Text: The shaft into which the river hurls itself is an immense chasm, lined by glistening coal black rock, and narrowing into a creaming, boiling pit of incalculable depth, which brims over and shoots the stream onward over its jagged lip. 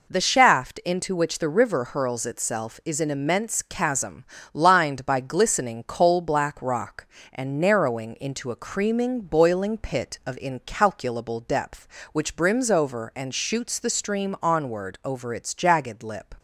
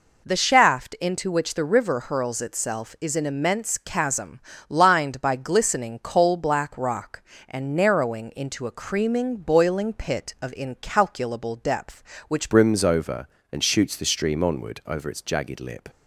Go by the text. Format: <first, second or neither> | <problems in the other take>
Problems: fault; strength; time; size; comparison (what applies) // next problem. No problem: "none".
first | changes voice at "brims"; from 12.4 s on; 3.4 s long